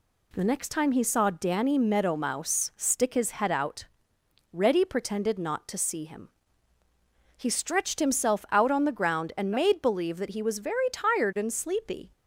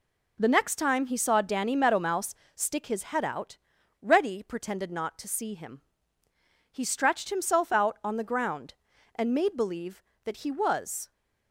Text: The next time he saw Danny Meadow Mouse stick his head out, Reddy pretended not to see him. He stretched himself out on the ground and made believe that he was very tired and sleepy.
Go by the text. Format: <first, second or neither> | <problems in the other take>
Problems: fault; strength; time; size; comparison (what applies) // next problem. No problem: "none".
first | pauses between "Mouse" and "stick"; slight; at 2.3 s; 0.22 s long // stops before "very tired and sleepy"; at 11.1 s